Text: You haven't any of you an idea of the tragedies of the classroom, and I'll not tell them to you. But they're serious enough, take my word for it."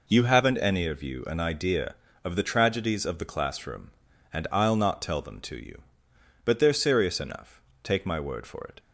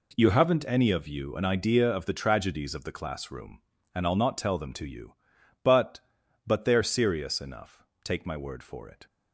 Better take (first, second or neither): first